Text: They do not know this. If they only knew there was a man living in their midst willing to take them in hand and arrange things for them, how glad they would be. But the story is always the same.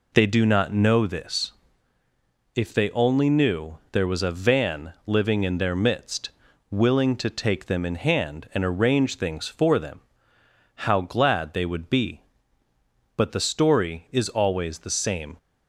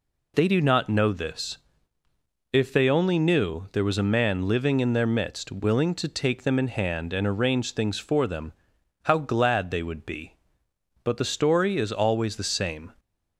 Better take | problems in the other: second | says "van" for "man"; at 4.3 s // pauses between "midst" and "willing"; at 6.2 s; 0.42 s long

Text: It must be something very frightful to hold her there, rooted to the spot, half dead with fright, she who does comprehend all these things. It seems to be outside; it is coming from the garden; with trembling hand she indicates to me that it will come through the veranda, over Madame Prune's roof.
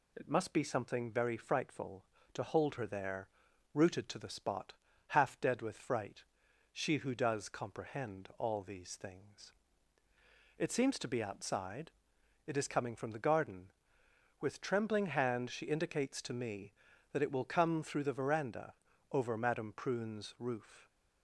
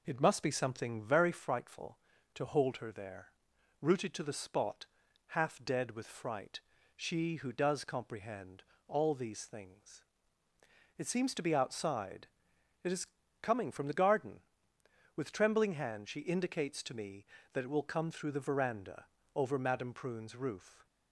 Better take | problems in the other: first | starts louder than the rest; noticeable; until 1.3 s; 4.5 dB // pauses between "comprehend" and "all"; slight; at 8.6 s; 0.24 s long // pauses between "is" and "coming"; slight; at 13.0 s; 0.34 s long

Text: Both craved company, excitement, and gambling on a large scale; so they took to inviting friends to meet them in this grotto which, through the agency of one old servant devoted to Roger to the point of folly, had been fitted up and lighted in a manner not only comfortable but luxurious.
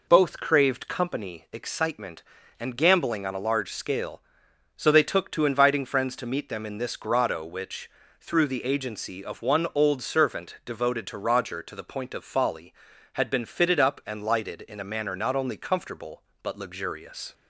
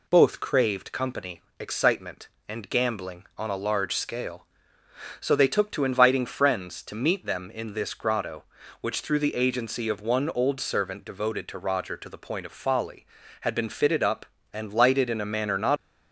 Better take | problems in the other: first | stops before "only comfortable but luxurious"; at 15.7 s

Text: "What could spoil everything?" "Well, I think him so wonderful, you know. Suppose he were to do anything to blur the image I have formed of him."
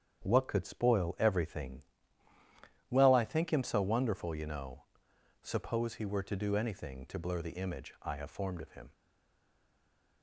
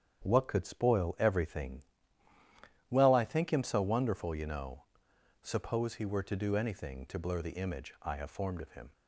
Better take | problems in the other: second | starts louder than the rest; strong; until 1.2 s; 8.5 dB; strong in the second // stays silent after the last word; noticeable; from 8.9 s on; 1.3 s long

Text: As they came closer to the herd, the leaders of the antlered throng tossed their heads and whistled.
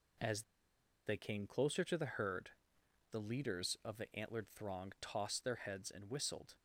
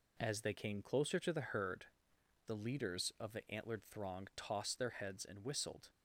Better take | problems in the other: second | pauses between "As" and "they"; noticeable; at 0.4 s; 0.63 s long

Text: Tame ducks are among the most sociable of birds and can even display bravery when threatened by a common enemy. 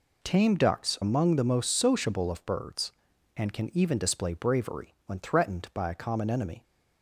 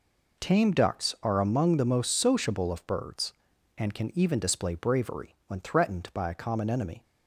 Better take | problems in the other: second | skips "are"; at 1.0 s

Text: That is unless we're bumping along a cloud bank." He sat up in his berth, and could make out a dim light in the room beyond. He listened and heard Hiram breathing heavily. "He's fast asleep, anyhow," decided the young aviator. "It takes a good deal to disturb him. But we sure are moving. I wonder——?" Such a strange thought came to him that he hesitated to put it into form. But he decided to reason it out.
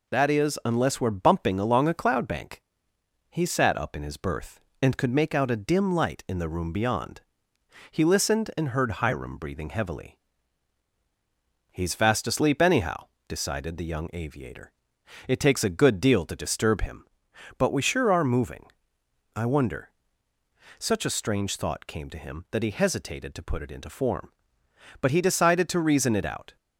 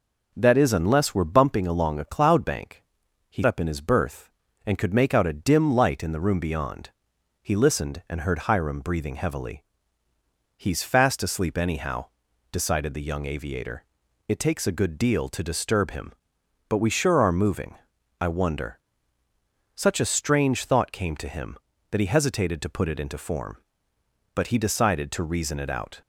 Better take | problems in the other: first | skips "sat"; at 3.4 s

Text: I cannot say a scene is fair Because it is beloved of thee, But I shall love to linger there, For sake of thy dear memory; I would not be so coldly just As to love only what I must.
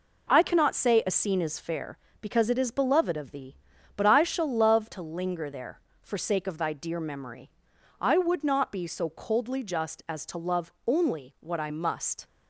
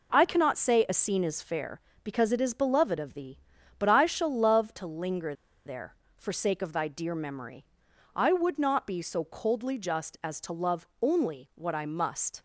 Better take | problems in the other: first | pauses between "linger" and "there"; slight; at 5.3 s; 0.32 s long

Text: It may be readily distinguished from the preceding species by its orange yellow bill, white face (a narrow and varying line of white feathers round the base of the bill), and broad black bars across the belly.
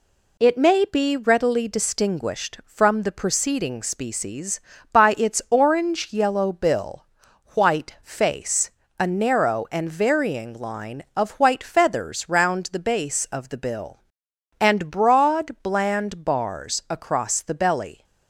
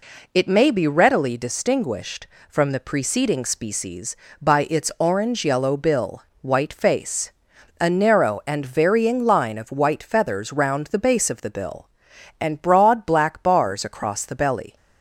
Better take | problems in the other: second | says "bland" for "black"; at 15.6 s

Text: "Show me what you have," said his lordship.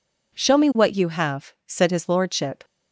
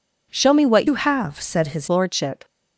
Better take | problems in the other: first | changes voice from "you" to "his"; from 0.8 to 1.8 s; 1.0 s long

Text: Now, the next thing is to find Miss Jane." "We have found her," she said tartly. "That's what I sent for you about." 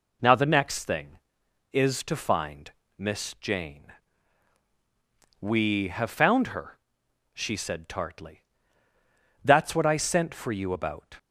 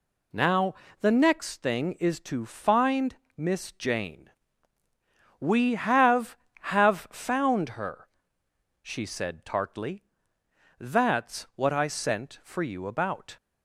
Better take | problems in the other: first | pauses between "find" and "Miss"; slight; at 3.1 s; 0.20 s long; slight in the first // says "have" twice; at 6.6 s

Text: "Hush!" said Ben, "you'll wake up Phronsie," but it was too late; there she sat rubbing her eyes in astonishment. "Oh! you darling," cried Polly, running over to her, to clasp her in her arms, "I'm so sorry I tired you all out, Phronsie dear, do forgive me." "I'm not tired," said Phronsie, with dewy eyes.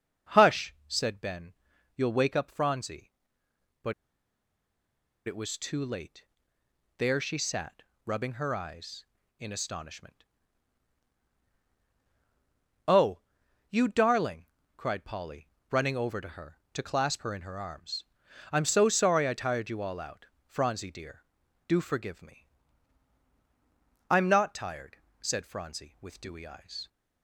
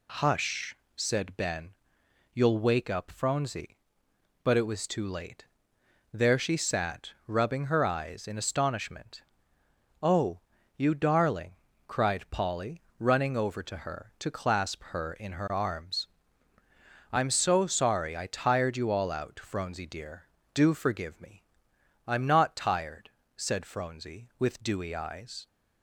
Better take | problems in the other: second | starts louder than the rest; until 1.4 s; 6.5 dB // pauses between "but" and "it"; strong; at 3.9 s; 1.3 s long // pauses between "sat" and "rubbing"; slight; at 7.8 s; 0.24 s long; slight in the second

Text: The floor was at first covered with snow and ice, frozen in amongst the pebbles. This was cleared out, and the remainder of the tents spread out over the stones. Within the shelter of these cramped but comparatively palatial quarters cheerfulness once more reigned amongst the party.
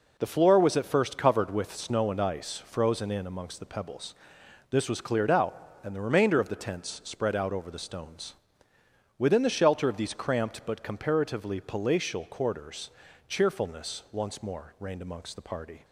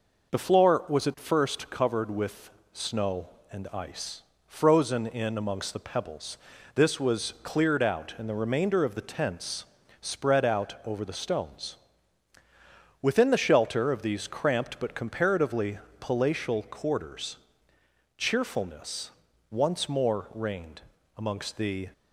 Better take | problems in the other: first | pauses between "with" and "snow"; slight; at 2.4 s; 0.22 s long // pauses between "tents" and "spread"; slight; at 9.6 s; 0.36 s long // pauses between "comparatively" and "palatial"; slight; at 15.7 s; 0.22 s long // pauses between "quarters" and "cheerfulness"; noticeable; at 17.3 s; 0.78 s long; slight in the first // pauses between "cheerfulness" and "once"; at 19.0 s; 0.40 s long // pauses between "reigned" and "amongst"; slight; at 20.8 s; 0.34 s long // stops before "party"; at 21.9 s

